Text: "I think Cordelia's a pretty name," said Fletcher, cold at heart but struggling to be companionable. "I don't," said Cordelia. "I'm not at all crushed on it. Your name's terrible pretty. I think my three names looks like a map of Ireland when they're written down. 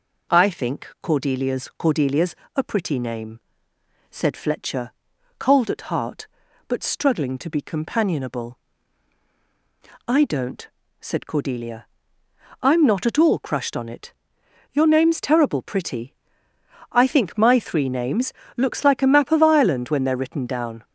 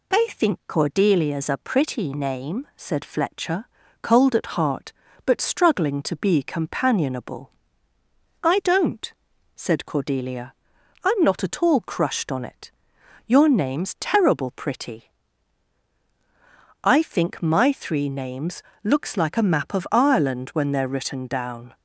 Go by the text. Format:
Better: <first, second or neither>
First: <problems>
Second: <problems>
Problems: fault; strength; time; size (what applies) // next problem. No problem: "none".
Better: second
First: says "Cordelia's" twice; at 1.7 s // pauses between "names" and "looks"; slight; at 18.3 s; 0.24 s long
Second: pauses between "names" and "looks"; slight; at 18.6 s; 0.20 s long